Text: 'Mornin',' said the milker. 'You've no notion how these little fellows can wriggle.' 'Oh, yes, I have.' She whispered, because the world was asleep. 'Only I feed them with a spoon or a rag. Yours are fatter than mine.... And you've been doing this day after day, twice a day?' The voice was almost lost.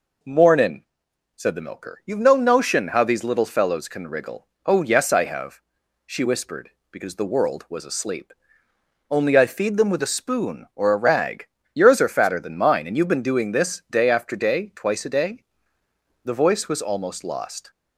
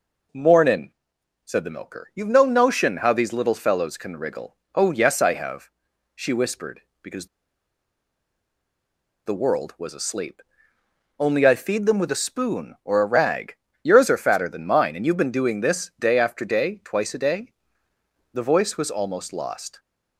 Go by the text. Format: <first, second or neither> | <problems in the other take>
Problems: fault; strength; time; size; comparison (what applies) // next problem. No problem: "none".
first | pauses between "because" and "the"; strong; at 7.2 s; 2.0 s long